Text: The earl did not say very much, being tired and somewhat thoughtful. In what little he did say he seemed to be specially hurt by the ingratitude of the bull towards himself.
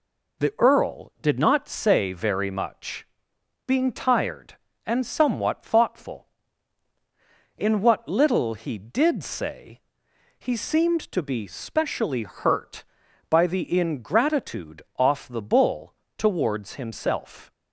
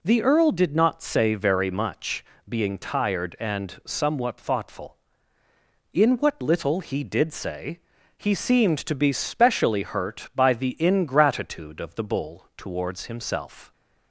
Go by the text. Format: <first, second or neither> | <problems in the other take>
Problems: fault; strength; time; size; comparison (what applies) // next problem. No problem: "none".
second | pauses between "say" and "he"; noticeable; at 9.7 s; 0.58 s long; also in the second // says "off" for "of"; at 14.9 s // pauses between "bull" and "towards"; slight; at 15.9 s; 0.22 s long